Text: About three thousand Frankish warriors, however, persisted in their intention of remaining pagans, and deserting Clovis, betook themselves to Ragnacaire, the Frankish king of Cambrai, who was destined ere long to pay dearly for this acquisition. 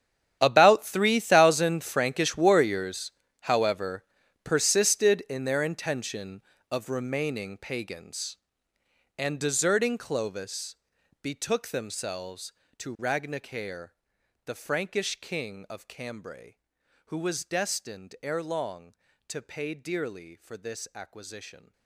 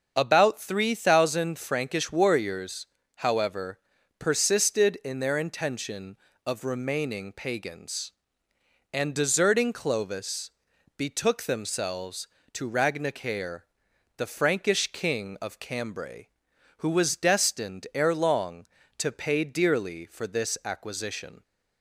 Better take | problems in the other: second | gets quieter; strong; throughout; 17 dB // starts louder than the rest; strong; until 1.4 s; 10 dB; also in the second

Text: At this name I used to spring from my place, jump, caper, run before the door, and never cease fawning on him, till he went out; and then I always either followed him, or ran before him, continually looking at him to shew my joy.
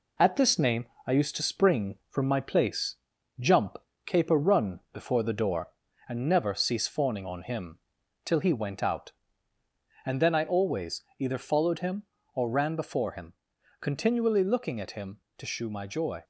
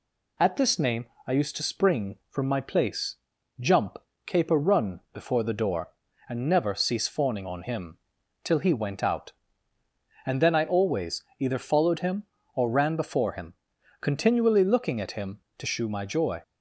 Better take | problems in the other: second | gets quieter; throughout; 3.5 dB // pauses between "name" and "I"; slight; at 0.8 s; 0.22 s long; slight in the second // pauses between "always" and "either"; slight; at 11.0 s; 0.16 s long; slight in the second

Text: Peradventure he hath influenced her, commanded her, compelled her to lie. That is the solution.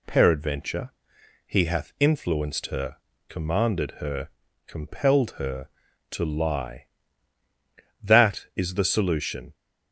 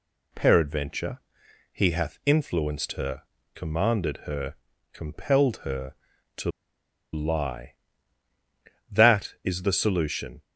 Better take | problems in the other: first | pauses between "Peradventure" and "he"; noticeable; at 1.1 s; 0.54 s long; noticeable in the first // pauses between "to" and "lie"; noticeable; at 6.4 s; 0.63 s long

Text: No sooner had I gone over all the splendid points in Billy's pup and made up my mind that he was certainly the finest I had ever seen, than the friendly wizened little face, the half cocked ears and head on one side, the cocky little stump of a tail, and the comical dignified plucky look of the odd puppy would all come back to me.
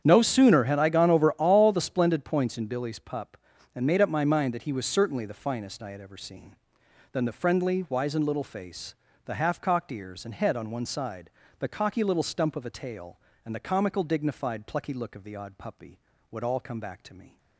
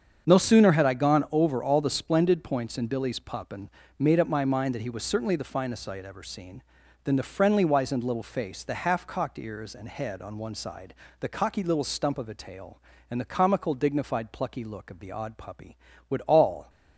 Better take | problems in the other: first | starts louder than the rest; strong; until 1.3 s; 7 dB; strong in the first // pauses between "and" and "made"; slight; at 3.6 s; 0.30 s long // stops before "come back to me"; at 16.6 s

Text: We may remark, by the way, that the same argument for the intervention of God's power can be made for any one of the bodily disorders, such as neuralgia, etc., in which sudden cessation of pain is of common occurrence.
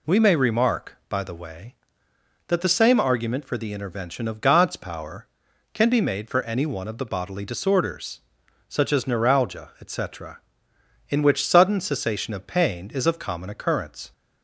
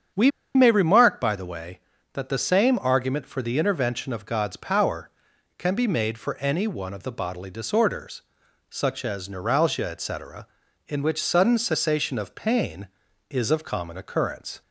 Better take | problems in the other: first | starts louder than the rest; strong; until 1.4 s; 7.5 dB // pauses between "We" and "may"; slight; at 0.2 s; 0.26 s long

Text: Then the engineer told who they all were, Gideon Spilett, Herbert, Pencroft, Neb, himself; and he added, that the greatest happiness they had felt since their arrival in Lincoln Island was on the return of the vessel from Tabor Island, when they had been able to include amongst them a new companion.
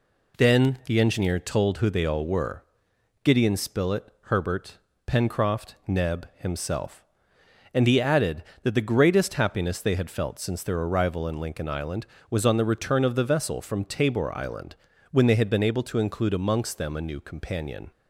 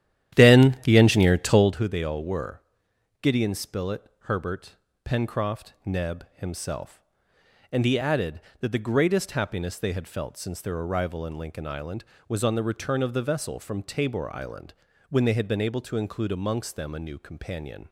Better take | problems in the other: first | starts louder than the rest; strong; until 1.8 s; 11.5 dB

